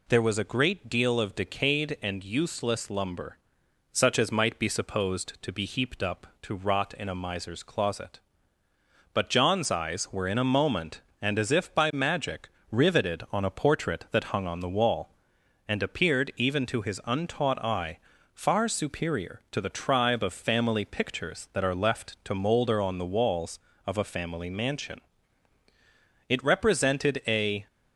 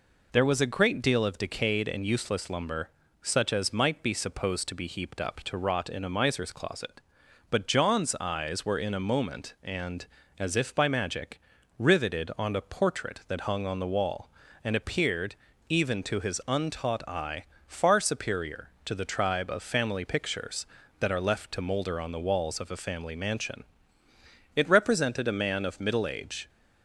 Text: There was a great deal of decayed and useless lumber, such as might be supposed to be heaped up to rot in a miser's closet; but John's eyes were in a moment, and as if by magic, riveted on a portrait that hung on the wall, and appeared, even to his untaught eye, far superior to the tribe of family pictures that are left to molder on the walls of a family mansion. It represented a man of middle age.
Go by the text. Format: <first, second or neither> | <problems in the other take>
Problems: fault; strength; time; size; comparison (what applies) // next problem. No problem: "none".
second | stops before "man of middle age"; at 27.6 s